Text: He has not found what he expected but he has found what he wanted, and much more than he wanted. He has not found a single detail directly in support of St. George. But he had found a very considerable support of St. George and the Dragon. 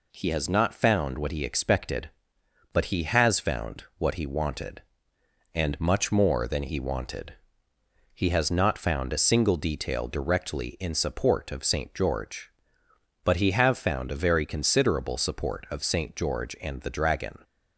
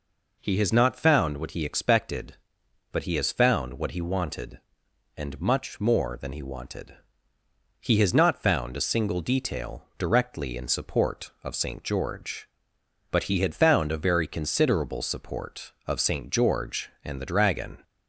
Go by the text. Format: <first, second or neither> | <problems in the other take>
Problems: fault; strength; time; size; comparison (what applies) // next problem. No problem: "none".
second | says "have" for "had"; at 13.5 s